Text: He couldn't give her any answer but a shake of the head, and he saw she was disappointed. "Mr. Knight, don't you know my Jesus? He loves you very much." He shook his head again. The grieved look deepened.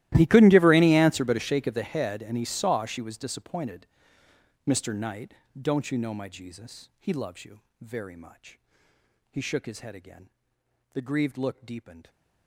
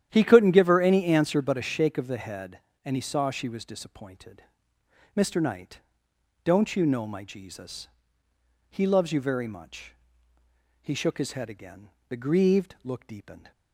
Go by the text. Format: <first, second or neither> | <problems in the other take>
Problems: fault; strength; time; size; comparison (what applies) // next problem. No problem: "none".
second | gets quieter; strong; throughout; 22.5 dB // starts louder than the rest; strong; until 1.1 s; 15.5 dB; strong in the second // pauses between "you" and "very"; slight; at 7.6 s; 0.20 s long